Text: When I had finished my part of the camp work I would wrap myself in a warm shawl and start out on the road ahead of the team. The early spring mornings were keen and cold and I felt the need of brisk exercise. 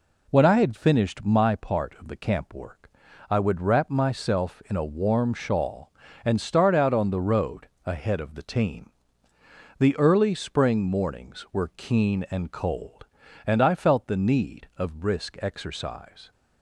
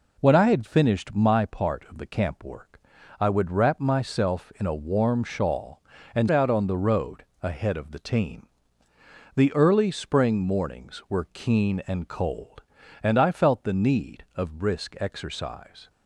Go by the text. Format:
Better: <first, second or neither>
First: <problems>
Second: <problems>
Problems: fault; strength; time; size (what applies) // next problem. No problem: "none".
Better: first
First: pauses between "work" and "I"; at 2.9 s; 0.40 s long // pauses between "road" and "ahead"; slight; at 7.6 s; 0.20 s long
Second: pauses between "work" and "I"; at 2.8 s; 0.40 s long // skips "start"; at 6.2 s // pauses between "road" and "ahead"; slight; at 7.2 s; 0.20 s long